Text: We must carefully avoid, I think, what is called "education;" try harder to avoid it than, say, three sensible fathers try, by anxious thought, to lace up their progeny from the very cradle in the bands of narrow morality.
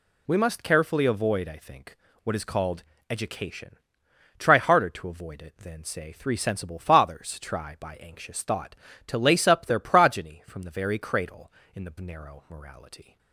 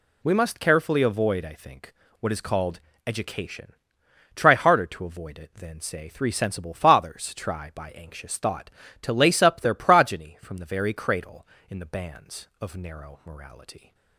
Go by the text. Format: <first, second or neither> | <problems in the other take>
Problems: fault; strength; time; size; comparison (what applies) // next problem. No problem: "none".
second | pauses between "called" and "education"; slight; at 2.8 s; 0.30 s long; slight in the second // skips "bands of"; at 11.9 s